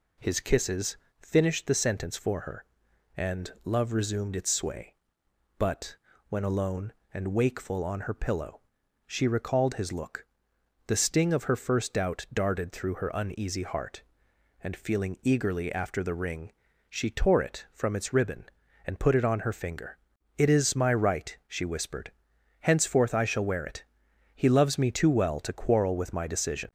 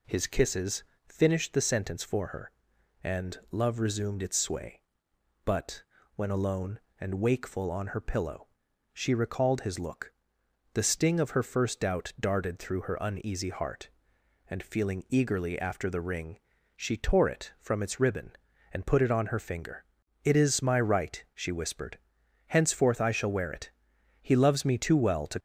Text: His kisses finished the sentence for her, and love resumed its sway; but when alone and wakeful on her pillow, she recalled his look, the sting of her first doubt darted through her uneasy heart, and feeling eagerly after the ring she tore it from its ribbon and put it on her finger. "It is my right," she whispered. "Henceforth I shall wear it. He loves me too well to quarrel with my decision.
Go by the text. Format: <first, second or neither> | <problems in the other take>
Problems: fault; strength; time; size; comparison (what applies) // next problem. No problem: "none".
first | pauses between "kisses" and "finished"; slight; at 0.8 s; 0.24 s long; slight in the first // pauses between "but" and "when"; slight; at 5.8 s; 0.32 s long; slight in the first // pauses between "ring" and "she"; at 16.3 s; 0.38 s long; also in the first // stops before "quarrel with my decision"; at 25.3 s